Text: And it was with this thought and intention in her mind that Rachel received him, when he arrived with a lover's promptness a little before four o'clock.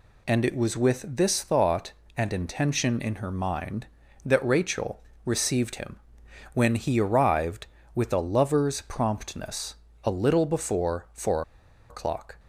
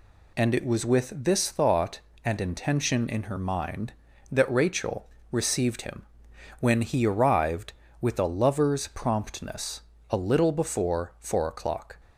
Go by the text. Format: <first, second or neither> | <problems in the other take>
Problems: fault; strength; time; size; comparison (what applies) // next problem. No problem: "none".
second | pauses between "Rachel" and "received"; slight; at 5.0 s; 0.24 s long; slight in the second // pauses between "promptness" and "a"; slight; at 9.7 s; 0.28 s long; slight in the second // pauses between "four" and "o'clock"; noticeable; at 11.4 s; 0.48 s long